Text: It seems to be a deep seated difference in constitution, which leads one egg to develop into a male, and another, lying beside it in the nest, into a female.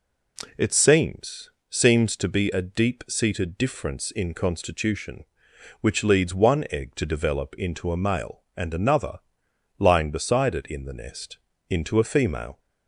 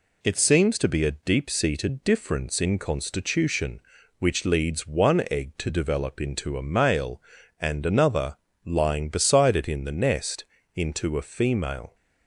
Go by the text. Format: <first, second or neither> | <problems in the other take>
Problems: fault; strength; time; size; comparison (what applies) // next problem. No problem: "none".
second | says "seems" twice; at 1.6 s